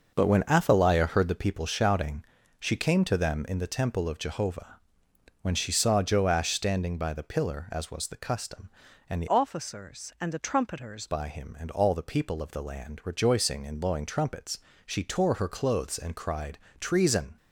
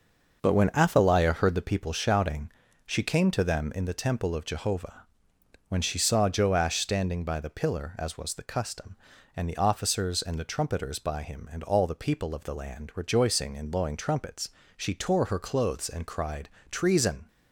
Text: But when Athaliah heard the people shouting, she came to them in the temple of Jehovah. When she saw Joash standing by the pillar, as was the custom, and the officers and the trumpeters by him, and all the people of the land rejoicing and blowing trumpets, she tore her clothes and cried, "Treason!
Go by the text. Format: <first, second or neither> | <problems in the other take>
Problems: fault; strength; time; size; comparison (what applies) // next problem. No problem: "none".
second | changes voice from "officers" to "trumpeters"; from 9.2 to 11.0 s; 1.8 s long